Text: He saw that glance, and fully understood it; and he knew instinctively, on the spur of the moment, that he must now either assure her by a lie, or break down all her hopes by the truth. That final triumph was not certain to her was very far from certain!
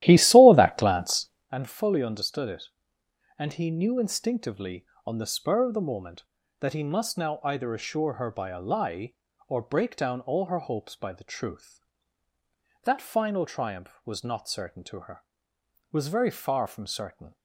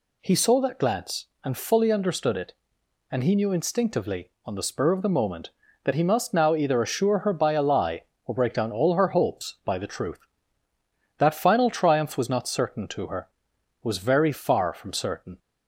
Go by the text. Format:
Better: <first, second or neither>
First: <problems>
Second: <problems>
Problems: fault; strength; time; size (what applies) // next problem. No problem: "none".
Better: second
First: starts louder than the rest; strong; until 1.5 s; 14 dB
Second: none